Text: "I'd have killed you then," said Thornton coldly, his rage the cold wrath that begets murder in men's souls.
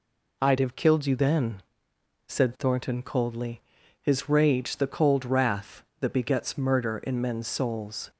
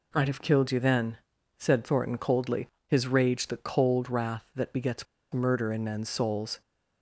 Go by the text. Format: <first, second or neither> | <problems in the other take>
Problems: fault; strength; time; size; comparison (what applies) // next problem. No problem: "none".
first | pauses between "begets" and "murder"; slight; at 5.0 s; 0.27 s long